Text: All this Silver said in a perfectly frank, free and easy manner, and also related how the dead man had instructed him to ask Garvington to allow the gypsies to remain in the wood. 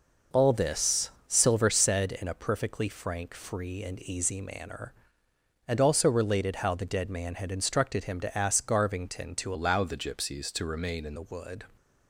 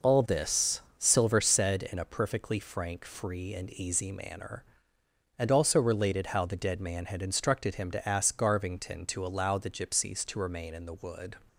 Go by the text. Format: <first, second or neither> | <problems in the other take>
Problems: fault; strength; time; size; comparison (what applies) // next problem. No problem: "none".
second | pauses between "this" and "Silver"; slight; at 1.0 s; 0.18 s long; slight in the second // changes voice from "allow" to "in"; from 9.5 to 11.1 s; 1.6 s long